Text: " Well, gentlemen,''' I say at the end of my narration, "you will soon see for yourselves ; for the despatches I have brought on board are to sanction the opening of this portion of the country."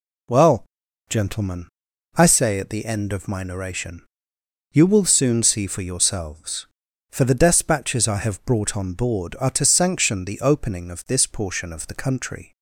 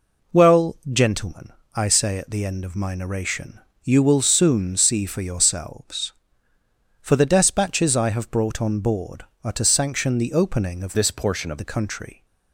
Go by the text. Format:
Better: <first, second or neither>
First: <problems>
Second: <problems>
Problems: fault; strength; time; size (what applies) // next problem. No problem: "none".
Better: first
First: none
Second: changes voice from "this" to "of"; from 10.9 to 11.5 s; 0.6 s long